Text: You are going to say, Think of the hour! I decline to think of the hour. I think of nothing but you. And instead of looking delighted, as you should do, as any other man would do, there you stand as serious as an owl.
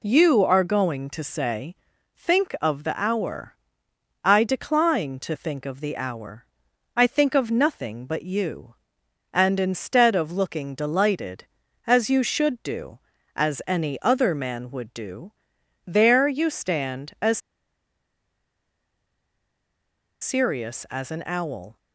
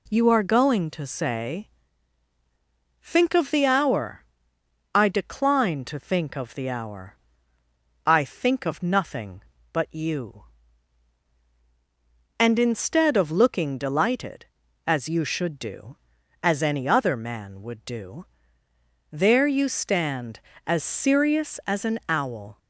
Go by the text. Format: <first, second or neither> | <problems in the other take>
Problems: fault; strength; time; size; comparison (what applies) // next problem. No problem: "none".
second | pauses between "as" and "serious"; strong; at 17.3 s; 2.8 s long